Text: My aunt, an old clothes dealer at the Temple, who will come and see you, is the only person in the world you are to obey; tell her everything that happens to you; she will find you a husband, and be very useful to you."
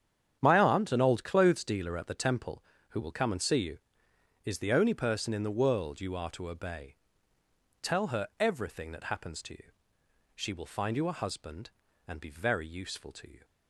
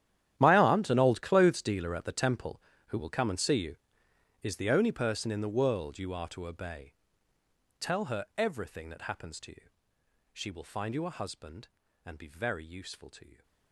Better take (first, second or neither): first